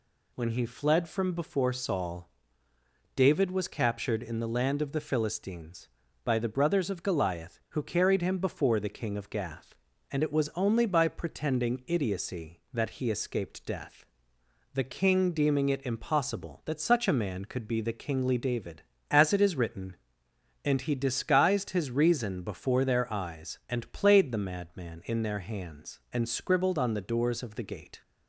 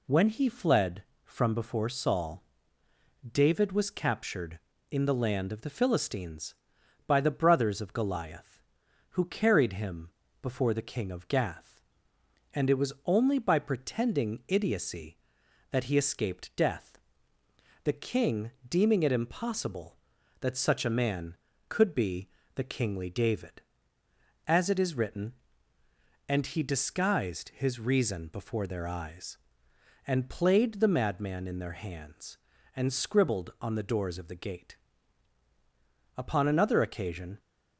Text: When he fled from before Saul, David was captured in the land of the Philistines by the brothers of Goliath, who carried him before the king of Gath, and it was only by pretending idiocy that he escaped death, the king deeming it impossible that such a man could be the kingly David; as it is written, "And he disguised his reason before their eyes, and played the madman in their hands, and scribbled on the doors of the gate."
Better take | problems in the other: first | pauses between "him" and "before"; slight; at 10.0 s; 0.32 s long // pauses between "king" and "deeming"; slight; at 18.5 s; 0.16 s long // pauses between "be" and "the"; slight; at 22.2 s; 0.28 s long // goes on to say "Upon another occasion"; noticeable; from 36.1 s on; 1.2 s long

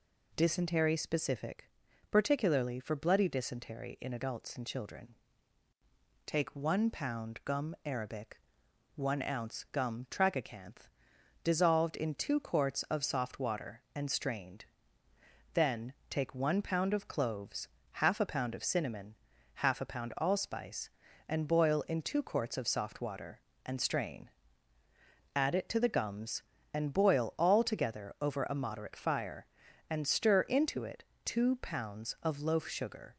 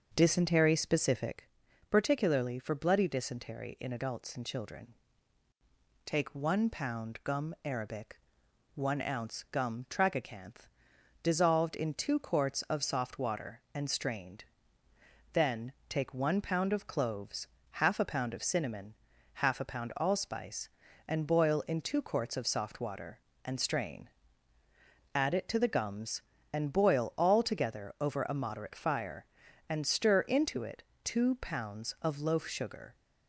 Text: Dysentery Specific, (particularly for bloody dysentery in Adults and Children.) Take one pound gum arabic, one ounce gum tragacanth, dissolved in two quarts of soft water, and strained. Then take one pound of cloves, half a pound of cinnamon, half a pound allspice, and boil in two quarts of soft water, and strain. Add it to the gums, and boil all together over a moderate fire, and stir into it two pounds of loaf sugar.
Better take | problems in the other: first | starts louder than the rest; until 1.4 s; 6.5 dB // pauses between "Then" and "take"; slight; at 15.7 s; 0.16 s long; slight in the first // pauses between "it" and "two"; slight; at 30.8 s; 0.22 s long; slight in the first

